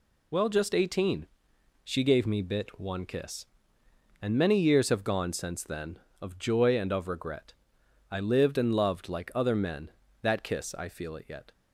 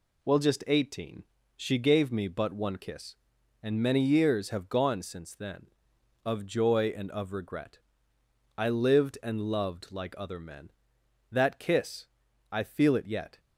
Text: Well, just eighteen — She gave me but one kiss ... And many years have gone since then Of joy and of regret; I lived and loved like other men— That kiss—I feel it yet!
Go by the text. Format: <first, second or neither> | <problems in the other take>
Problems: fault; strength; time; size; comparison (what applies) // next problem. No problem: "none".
second | says "bit" for "but"; at 2.4 s